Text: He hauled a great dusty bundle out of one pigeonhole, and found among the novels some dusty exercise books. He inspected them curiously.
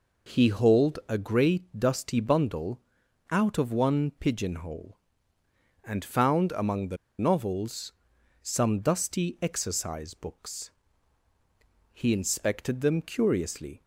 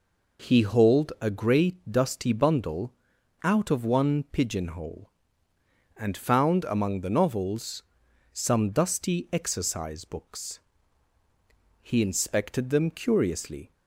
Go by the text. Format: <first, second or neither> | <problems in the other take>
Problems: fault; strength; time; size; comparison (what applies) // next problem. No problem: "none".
second | pauses between "bundle" and "out"; noticeable; at 2.8 s; 0.50 s long; noticeable in the second // pauses between "the" and "novels"; slight; at 6.9 s; 0.22 s long // pauses between "novels" and "some"; noticeable; at 7.9 s; 0.48 s long; noticeable in the second